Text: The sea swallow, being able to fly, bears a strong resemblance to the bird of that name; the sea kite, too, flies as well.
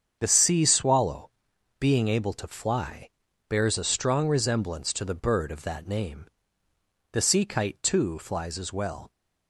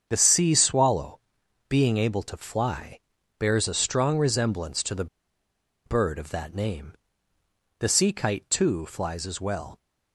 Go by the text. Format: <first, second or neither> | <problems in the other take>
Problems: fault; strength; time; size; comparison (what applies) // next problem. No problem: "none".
first | starts louder than the rest; strong; until 1.1 s; 7.5 dB; strong in the first // pauses between "the" and "bird"; noticeable; at 5.0 s; 0.80 s long